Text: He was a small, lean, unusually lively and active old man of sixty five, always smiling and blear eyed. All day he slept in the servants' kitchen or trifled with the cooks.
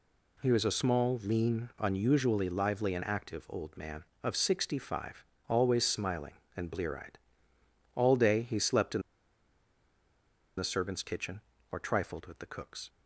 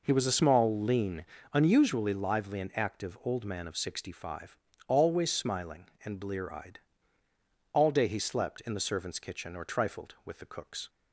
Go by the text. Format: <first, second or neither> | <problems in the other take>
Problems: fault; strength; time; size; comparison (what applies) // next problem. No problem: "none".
second | pauses between "in" and "the"; strong; at 9.0 s; 1.5 s long